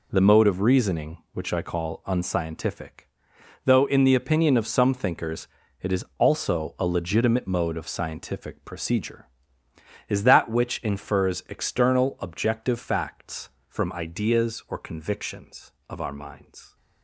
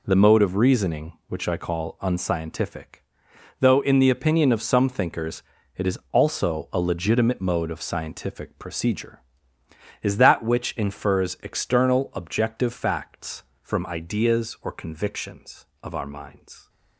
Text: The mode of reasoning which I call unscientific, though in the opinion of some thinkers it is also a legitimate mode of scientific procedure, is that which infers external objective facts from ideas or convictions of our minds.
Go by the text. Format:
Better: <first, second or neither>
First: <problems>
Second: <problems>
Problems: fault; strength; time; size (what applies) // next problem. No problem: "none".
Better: neither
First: pauses between "thinkers" and "it"; slight; at 5.4 s; 0.36 s long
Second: pauses between "thinkers" and "it"; slight; at 5.4 s; 0.36 s long